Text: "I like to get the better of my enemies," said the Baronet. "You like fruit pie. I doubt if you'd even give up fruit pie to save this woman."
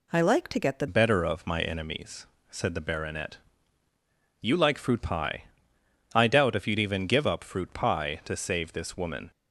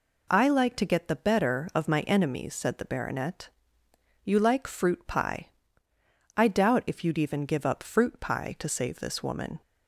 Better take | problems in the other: second | changes voice at "better"; from 0.8 s on; 8.5 s long

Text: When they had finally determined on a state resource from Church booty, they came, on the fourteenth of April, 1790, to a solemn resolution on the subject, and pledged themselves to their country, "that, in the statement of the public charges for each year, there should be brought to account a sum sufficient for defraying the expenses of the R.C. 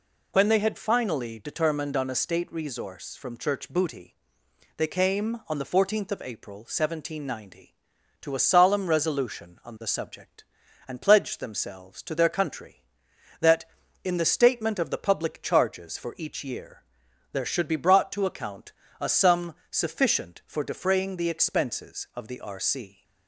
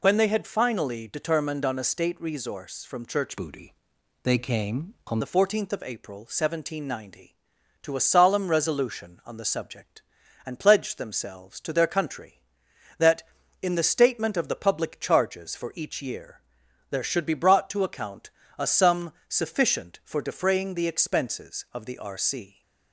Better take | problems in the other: first | changes voice from "booty" to "on"; from 3.3 to 5.2 s; 1.9 s long // pauses between "account" and "a"; slight; at 18.3 s; 0.26 s long; slight in the first // pauses between "sum" and "sufficient"; slight; at 19.1 s; 0.16 s long; slight in the first

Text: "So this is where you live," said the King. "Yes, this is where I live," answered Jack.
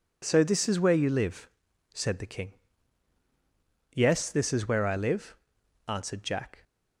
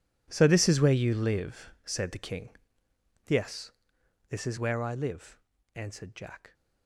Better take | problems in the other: first | gets quieter; strong; throughout; 17 dB

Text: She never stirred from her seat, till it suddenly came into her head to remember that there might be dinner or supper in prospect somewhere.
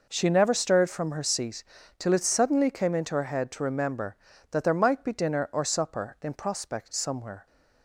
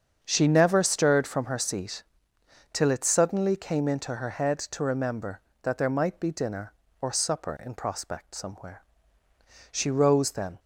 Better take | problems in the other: first | starts louder than the rest; strong; until 1.2 s; 7 dB // goes on to say "She rose then"; noticeable; from 9.7 s on; 0.88 s long

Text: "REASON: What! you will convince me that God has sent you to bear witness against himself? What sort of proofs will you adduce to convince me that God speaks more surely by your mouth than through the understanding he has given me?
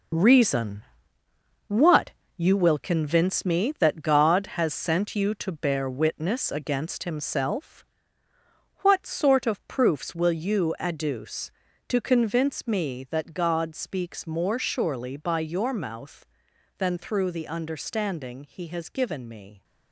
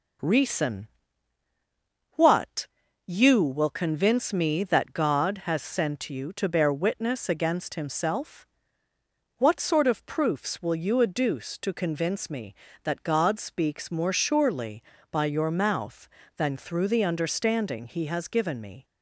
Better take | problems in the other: second | gets quieter; strong; throughout; 8 dB

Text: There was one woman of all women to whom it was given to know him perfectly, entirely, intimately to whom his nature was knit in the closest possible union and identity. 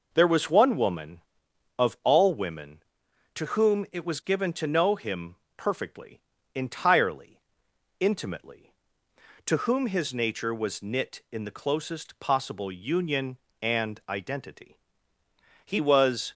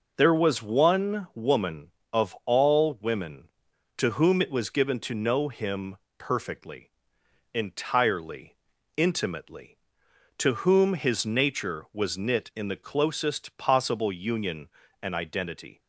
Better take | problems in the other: second | pauses between "him" and "perfectly"; slight; at 5.3 s; 0.22 s long; slight in the second // goes on to say "He was"; noticeable; from 15.6 s on; 0.68 s long

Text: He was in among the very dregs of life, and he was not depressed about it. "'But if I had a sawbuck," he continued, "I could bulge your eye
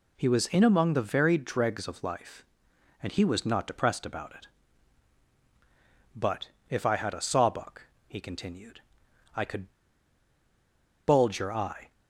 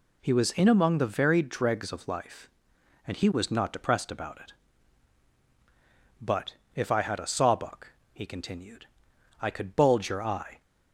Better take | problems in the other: second | pauses between "But" and "if"; slight; at 6.4 s; 0.20 s long; slight in the second // pauses between "could" and "bulge"; strong; at 9.7 s; 1.3 s long

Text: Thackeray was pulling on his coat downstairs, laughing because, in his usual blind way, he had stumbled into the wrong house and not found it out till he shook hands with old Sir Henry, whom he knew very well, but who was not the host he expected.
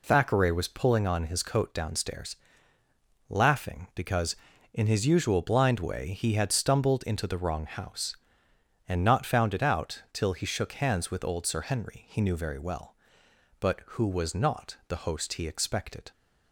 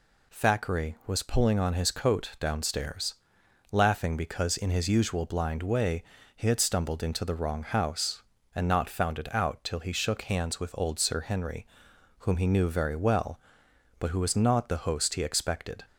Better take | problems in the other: second | skips "whom"; at 12.0 s

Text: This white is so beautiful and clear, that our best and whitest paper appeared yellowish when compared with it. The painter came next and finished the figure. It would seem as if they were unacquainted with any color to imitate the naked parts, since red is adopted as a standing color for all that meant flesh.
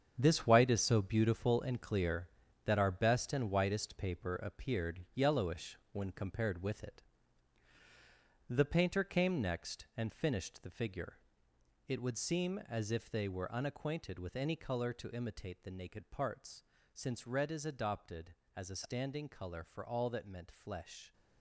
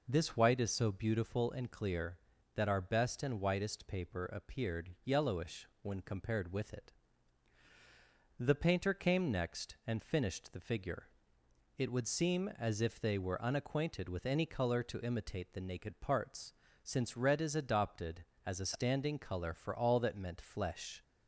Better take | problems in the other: second | gets quieter; strong; throughout; 10.5 dB // pauses between "yellowish" and "when"; slight; at 5.7 s; 0.16 s long; slight in the second

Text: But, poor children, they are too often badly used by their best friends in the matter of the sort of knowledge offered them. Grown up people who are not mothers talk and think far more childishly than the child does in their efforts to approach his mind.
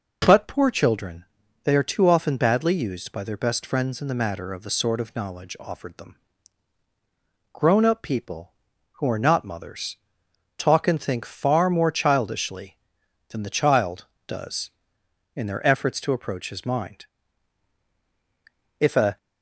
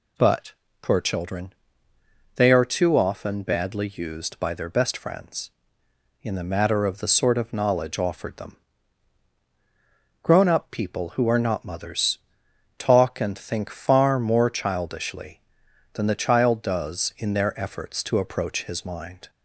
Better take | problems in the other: second | pauses between "mothers" and "talk"; noticeable; at 9.9 s; 0.60 s long; noticeable in the second // goes on to say "If a"; slight; from 18.7 s on; 0.38 s long

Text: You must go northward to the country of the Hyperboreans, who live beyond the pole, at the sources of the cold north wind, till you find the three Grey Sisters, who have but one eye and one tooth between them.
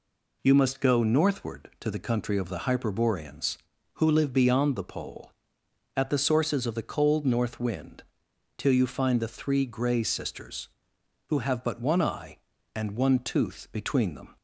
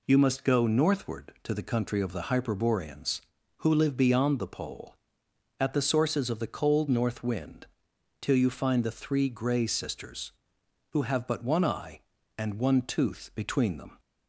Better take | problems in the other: neither | none

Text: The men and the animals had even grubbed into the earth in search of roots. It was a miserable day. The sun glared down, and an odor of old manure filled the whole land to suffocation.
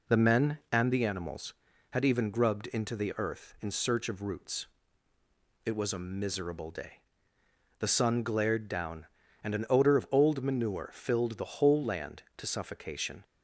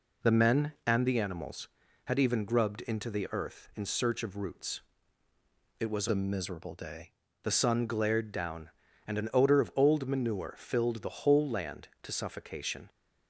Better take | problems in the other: first | changes voice from "a" to "day"; from 6.0 to 7.1 s; 1.1 s long

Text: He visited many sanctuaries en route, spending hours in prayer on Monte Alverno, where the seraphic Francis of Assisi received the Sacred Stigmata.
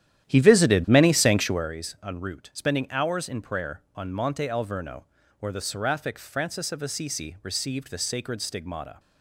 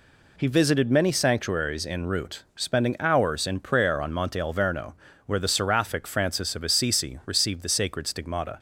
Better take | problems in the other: second | starts louder than the rest; strong; until 1.8 s; 11.5 dB

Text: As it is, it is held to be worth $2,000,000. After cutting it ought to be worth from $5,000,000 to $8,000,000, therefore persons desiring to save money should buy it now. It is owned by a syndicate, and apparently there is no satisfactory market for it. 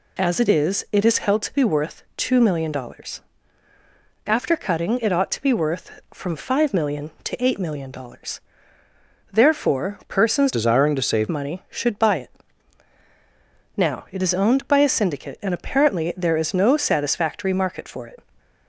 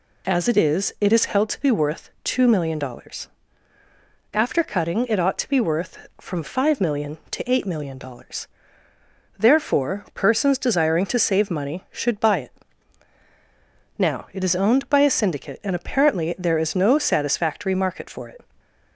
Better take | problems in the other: second | changes voice from "desiring" to "save"; from 10.5 to 11.2 s; 0.7 s long // pauses between "it" and "now"; strong; at 12.3 s; 1.4 s long; strong in the second

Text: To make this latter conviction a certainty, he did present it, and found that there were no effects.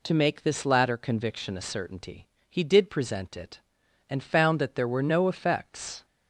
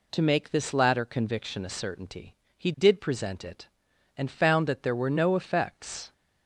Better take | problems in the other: neither | none

